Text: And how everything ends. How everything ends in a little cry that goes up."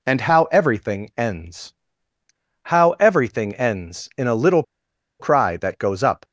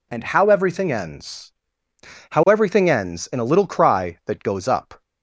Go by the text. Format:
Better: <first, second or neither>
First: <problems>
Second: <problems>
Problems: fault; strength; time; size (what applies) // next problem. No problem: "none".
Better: second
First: pauses between "little" and "cry"; noticeable; at 4.6 s; 0.56 s long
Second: none